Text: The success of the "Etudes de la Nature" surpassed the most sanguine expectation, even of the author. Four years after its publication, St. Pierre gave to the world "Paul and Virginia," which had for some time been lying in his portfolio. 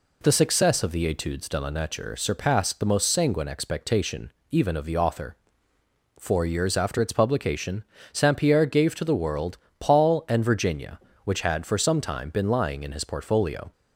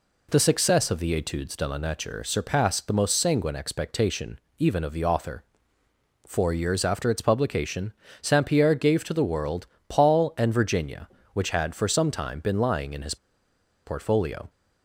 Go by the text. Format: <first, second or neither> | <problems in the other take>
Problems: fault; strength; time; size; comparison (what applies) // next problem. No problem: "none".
first | pauses between "world" and "Paul"; slight; at 9.6 s; 0.22 s long; slight in the first // pauses between "his" and "portfolio"; noticeable; at 13.1 s; 0.70 s long